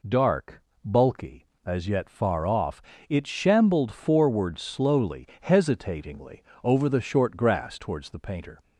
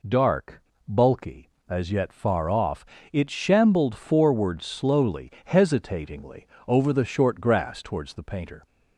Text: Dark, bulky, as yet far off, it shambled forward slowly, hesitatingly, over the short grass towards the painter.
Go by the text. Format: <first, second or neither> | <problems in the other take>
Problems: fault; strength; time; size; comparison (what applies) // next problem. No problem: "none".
neither | none